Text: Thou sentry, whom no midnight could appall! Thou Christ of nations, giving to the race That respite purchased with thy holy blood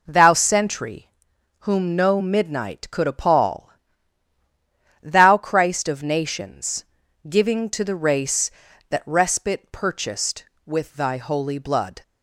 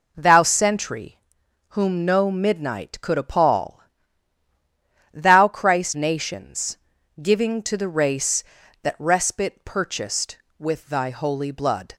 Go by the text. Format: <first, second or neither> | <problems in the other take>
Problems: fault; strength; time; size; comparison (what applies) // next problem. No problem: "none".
first | skips "of"; at 5.9 s